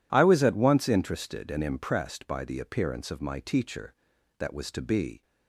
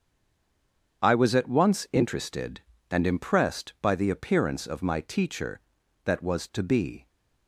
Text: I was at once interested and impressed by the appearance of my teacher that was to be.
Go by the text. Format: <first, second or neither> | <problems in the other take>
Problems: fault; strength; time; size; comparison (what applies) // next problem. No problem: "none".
first | stays silent before the first word; until 1.0 s; 1.0 s long // starts louder than the rest; strong; until 2.0 s; 8 dB